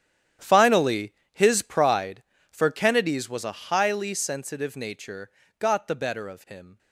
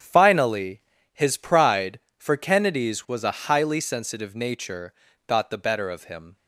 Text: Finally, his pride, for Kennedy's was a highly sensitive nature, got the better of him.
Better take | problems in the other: second | gets quieter; strong; throughout; 14.5 dB // starts louder than the rest; strong; until 1.6 s; 10 dB; strong in the second

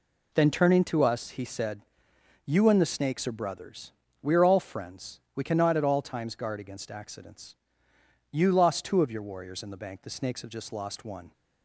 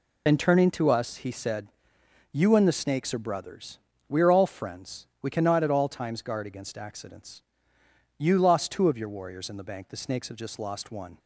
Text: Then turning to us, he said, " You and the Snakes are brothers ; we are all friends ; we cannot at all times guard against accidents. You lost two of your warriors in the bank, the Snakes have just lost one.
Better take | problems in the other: first | loses the start of "Then"; at 0.2 s; 55 ms

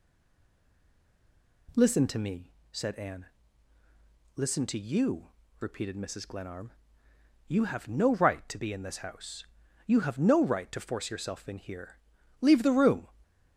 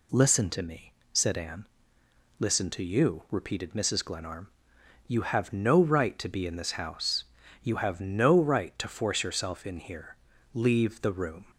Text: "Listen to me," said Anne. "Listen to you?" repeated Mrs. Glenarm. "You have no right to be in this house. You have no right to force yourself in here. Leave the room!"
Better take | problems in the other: second | stays silent before the first word; noticeable; until 1.6 s; 1.6 s long

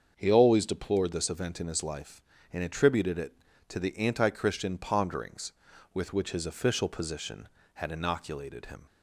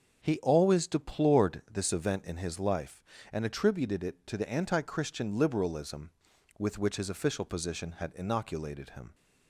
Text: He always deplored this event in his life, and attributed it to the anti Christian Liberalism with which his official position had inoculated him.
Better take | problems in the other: second | starts louder than the rest; until 1.1 s; 7 dB; also in the second // says "Ponderings" for "Liberalism"; at 4.7 s

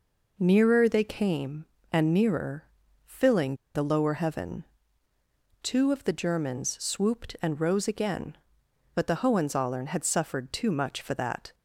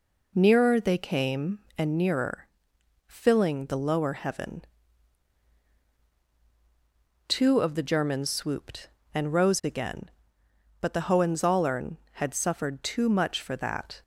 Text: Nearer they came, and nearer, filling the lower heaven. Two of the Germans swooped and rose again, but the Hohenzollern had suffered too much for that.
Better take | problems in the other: second | pauses between "filling" and "the"; slight; at 3.5 s; 0.21 s long

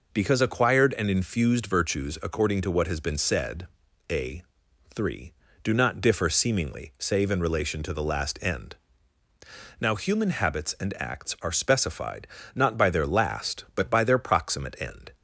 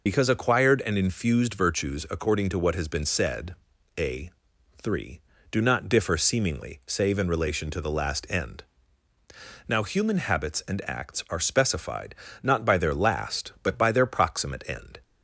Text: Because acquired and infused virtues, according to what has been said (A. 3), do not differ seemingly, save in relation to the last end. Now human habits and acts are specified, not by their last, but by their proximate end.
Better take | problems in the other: first | loses the start of "Because"; at 0.0 s; 60 ms

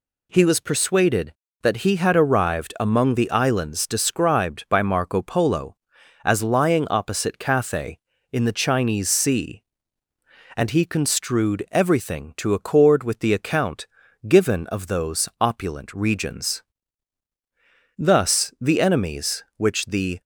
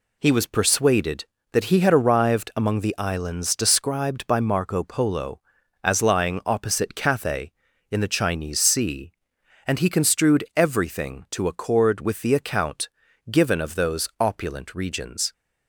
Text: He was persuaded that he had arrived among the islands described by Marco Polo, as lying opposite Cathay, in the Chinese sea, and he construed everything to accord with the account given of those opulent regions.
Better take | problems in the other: second | pauses between "account" and "given"; at 13.8 s; 0.40 s long; also in the second // goes on to say "Thus the enemies which the"; strong; from 17.9 s on; 2.2 s long

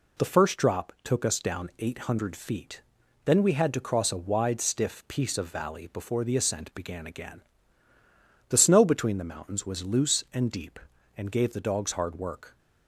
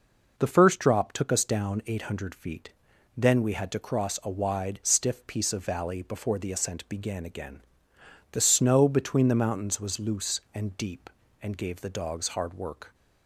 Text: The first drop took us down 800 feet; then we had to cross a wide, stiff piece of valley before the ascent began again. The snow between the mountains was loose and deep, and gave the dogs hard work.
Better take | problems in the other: neither | none

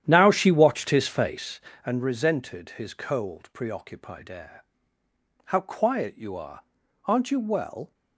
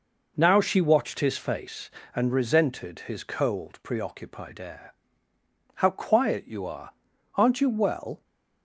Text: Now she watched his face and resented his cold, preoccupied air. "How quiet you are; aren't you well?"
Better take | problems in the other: second | starts louder than the rest; strong; until 1.6 s; 10.5 dB

